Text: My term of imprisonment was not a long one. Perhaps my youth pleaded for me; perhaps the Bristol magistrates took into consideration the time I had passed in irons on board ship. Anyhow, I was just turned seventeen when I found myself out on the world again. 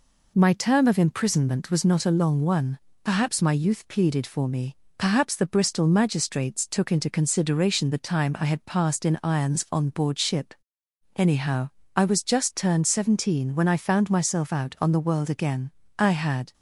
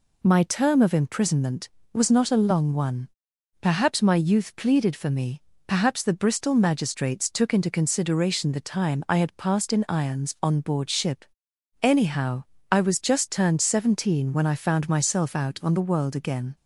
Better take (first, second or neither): second